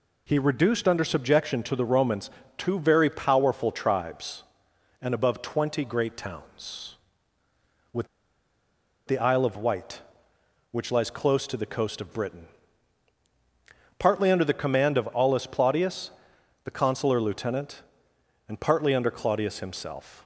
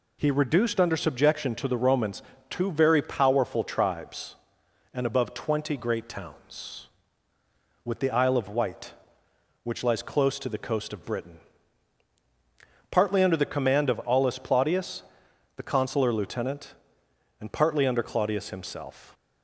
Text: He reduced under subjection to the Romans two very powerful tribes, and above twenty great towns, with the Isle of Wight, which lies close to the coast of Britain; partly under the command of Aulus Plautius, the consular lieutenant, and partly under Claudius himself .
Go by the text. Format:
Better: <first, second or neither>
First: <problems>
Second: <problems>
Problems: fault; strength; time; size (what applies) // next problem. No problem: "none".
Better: second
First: pauses between "Romans" and "two"; slight; at 2.2 s; 0.28 s long // pauses between "with" and "the"; at 8.0 s; 1.0 s long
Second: pauses between "Romans" and "two"; slight; at 2.2 s; 0.28 s long